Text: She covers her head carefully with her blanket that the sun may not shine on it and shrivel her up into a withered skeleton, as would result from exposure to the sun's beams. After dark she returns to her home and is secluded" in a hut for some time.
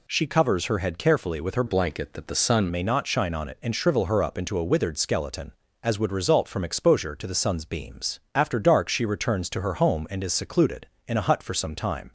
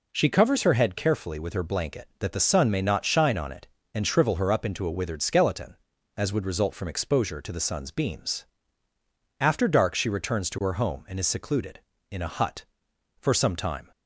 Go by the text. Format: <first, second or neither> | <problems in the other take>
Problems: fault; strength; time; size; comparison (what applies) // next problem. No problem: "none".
second | changes voice from "blanket" to "sun"; from 1.6 to 2.6 s; 1.0 s long